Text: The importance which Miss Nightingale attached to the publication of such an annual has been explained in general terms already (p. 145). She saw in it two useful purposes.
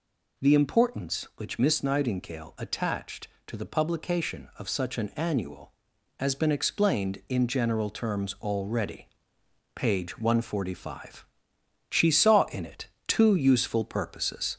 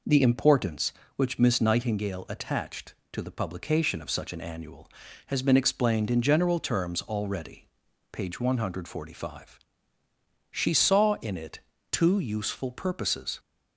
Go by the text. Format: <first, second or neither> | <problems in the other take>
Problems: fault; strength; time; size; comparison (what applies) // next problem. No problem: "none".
second | gets louder; slight; throughout; 2.5 dB // pauses between "it" and "two"; slight; at 12.8 s; 0.20 s long; slight in the second